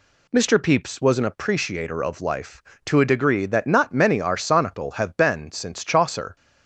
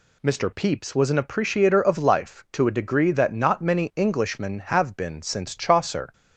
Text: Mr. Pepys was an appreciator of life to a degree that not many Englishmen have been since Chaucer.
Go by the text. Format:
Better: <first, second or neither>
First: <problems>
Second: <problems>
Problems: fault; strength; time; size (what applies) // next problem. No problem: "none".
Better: second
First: says "Arsonical" for "Englishmen"; at 4.1 s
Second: none